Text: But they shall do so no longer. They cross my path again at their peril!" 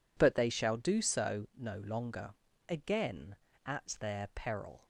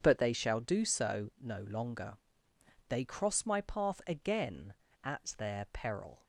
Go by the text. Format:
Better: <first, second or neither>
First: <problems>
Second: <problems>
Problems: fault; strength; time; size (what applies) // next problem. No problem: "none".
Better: second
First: skips "They cross my path"; at 2.5 s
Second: none